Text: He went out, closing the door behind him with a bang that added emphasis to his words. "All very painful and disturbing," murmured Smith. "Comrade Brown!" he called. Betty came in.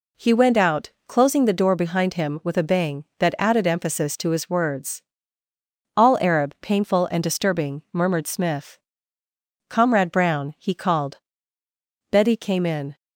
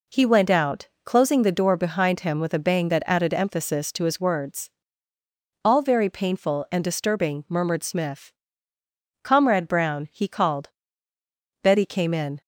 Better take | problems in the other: second | says "arab" for "very"; at 6.2 s

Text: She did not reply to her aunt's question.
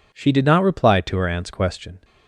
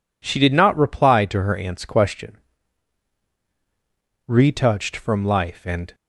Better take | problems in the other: first | goes on to say "Retouched from life and"; from 4.3 s on; 1.6 s long

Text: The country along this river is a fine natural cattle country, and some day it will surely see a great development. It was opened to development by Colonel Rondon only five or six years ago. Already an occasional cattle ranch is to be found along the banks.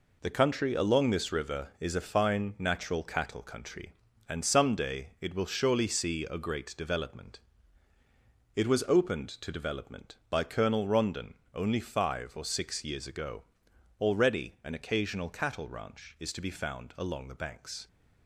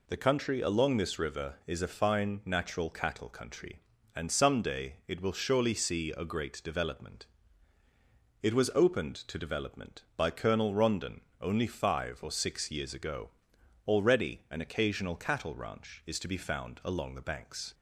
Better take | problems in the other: second | gets quieter; throughout; 7 dB // pauses between "Rondon" and "only"; slight; at 11.3 s; 0.18 s long; slight in the second

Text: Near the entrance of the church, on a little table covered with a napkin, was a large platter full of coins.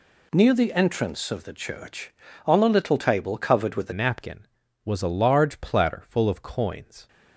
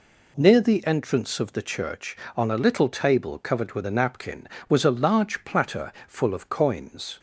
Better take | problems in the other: second | changes voice at "napkin"; from 3.9 s on; 3.1 s long

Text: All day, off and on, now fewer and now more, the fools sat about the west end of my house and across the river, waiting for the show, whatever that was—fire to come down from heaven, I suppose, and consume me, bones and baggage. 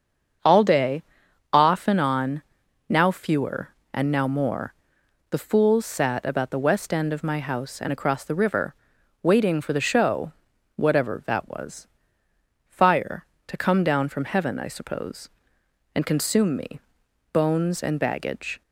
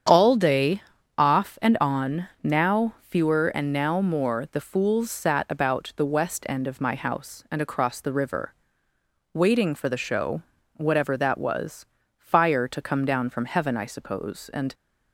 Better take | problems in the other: first | starts louder than the rest; strong; until 1.4 s; 8 dB; also in the first // stops before "consume me bones and baggage"; at 14.7 s

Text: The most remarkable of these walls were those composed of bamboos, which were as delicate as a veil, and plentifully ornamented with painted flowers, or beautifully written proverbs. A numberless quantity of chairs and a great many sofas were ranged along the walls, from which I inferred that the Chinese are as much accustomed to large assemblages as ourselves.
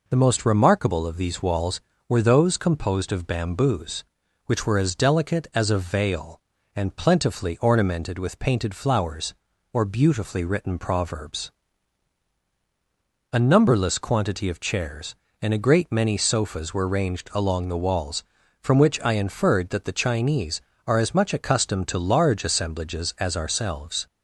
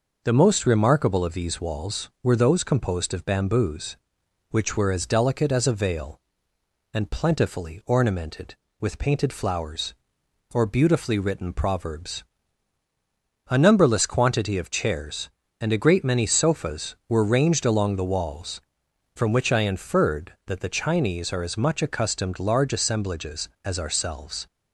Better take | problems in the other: first | skips "to"; at 22.3 s

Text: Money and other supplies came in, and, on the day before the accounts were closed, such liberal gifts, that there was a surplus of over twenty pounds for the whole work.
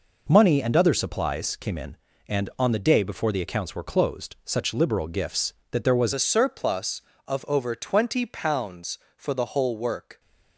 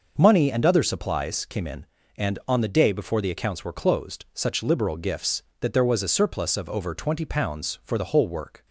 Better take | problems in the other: second | changes voice at "a"; from 6.1 s on; 4.0 s long

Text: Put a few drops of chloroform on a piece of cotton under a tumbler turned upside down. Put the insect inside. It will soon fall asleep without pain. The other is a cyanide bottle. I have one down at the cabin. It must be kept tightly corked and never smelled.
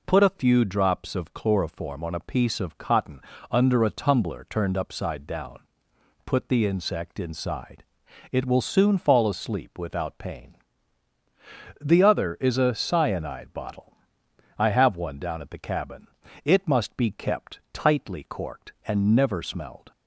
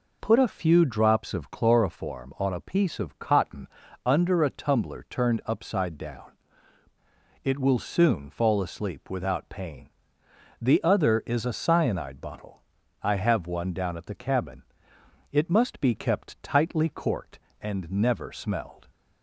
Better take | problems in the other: first | pauses between "cotton" and "under"; at 3.6 s; 0.38 s long; slight in the first // skips "Put the insect inside"; at 6.8 s

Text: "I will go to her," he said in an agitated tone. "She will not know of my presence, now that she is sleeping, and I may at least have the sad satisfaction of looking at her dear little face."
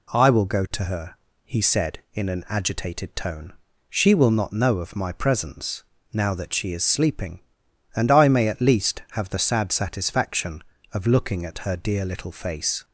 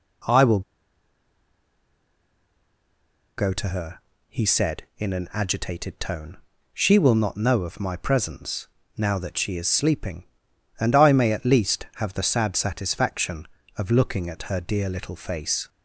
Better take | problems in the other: first | pauses between "will" and "go"; strong; at 0.6 s; 2.7 s long

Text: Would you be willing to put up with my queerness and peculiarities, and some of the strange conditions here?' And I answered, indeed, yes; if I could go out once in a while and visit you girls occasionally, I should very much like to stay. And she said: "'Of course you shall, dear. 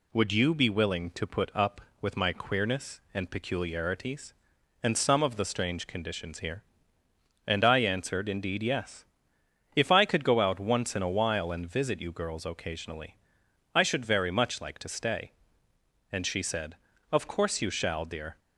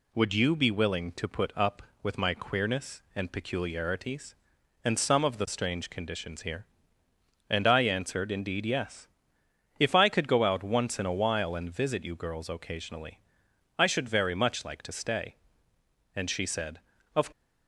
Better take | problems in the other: first | stops before "course you shall dear"; at 17.3 s

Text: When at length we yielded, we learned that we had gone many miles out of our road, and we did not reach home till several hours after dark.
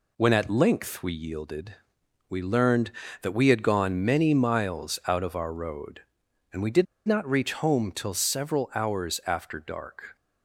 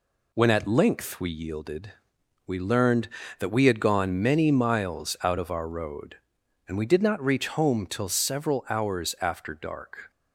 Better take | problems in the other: second | pauses between "did" and "not"; slight; at 6.8 s; 0.22 s long

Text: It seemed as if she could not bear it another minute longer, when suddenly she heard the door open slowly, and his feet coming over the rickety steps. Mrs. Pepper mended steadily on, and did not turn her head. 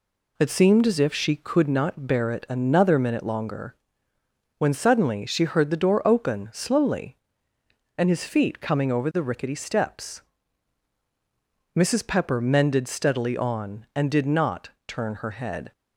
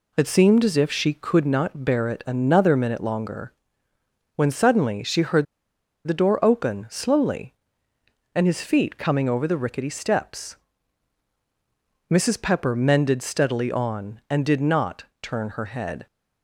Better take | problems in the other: first | pauses between "heard" and "the"; noticeable; at 5.4 s; 0.61 s long // pauses between "not" and "turn"; slight; at 15.0 s; 0.16 s long; slight in the first

